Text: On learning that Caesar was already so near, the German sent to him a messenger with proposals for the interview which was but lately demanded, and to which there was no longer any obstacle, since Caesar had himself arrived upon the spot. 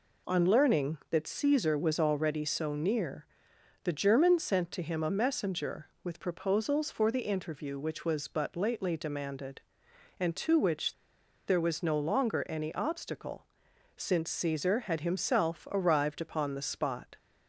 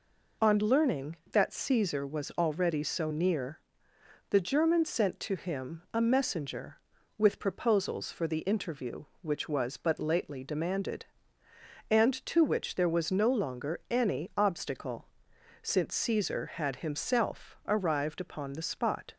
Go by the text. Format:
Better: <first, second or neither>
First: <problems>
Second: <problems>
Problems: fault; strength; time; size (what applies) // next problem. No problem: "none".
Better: second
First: pauses between "which" and "there"; noticeable; at 10.9 s; 0.53 s long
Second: none